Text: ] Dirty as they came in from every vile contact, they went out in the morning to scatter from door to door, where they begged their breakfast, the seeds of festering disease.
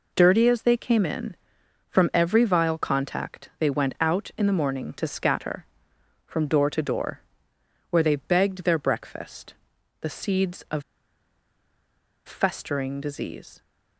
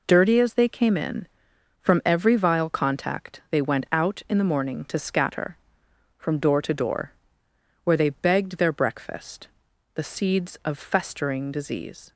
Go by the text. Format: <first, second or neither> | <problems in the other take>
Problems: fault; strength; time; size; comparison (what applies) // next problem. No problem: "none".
second | pauses between "of" and "festering"; strong; at 10.8 s; 1.4 s long